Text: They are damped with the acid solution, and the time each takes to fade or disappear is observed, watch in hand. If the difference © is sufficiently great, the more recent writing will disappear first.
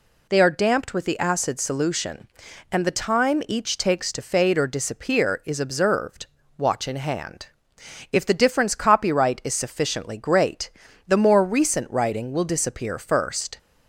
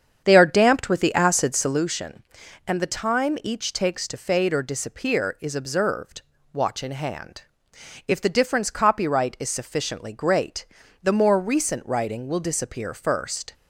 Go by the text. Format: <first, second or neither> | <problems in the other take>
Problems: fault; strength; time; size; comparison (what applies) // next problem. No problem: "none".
first | starts louder than the rest; strong; until 1.9 s; 8 dB